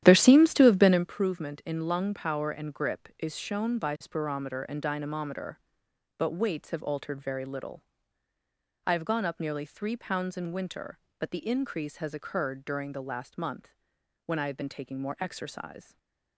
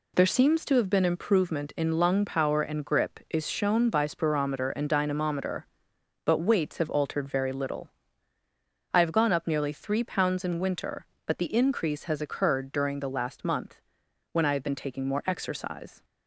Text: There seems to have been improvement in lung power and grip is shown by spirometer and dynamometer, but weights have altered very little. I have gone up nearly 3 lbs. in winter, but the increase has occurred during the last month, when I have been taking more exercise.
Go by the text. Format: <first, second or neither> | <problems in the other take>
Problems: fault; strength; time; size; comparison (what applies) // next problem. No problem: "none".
second | starts louder than the rest; strong; until 1.1 s; 11.5 dB // stays silent after the last word; slight; from 15.8 s on; 0.5 s long